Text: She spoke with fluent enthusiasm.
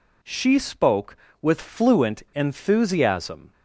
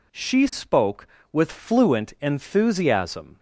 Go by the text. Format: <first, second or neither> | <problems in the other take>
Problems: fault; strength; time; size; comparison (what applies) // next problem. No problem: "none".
neither | none